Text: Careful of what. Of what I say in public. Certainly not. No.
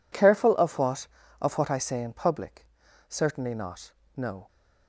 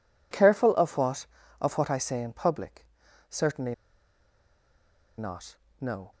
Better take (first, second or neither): first